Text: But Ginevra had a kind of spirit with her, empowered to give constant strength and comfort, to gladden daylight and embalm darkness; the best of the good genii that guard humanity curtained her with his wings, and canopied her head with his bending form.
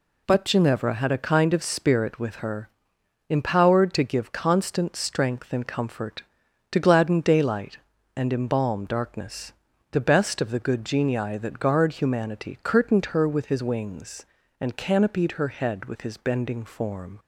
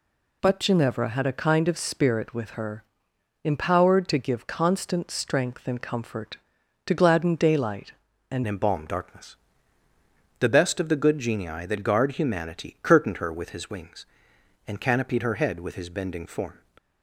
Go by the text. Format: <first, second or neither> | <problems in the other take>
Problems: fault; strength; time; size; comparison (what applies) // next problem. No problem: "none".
first | changes voice at "embalm"; from 8.4 s on; 8.1 s long